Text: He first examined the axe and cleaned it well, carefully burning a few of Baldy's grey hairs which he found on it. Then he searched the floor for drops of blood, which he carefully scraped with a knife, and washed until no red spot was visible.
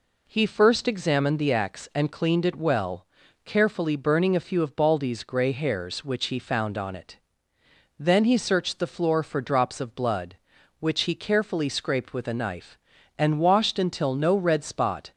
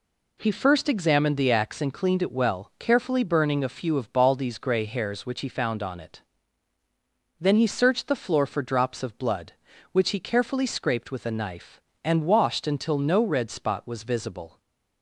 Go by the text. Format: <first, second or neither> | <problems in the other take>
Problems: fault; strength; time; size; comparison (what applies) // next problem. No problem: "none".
second | stops before "was visible"; at 15.1 s